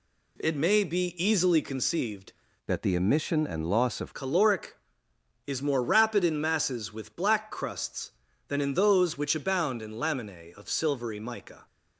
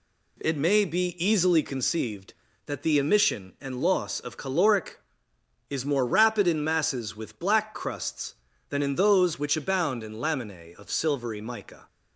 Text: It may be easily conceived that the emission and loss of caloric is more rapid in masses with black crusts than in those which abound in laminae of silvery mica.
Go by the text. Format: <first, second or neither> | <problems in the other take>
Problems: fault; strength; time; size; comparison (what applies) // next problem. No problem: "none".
second | changes voice from "that" to "of"; from 2.6 to 4.1 s; 1.5 s long